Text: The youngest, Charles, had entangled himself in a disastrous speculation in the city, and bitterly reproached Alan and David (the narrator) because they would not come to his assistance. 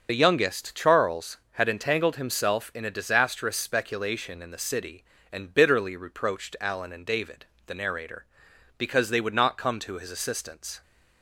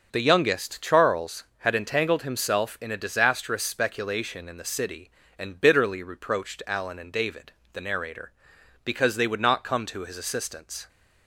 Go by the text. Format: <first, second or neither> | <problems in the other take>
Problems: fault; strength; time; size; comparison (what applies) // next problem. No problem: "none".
second | loses the start of "The"; at 0.0 s; 40 ms // starts louder than the rest; until 1.1 s; 6.5 dB; also in the second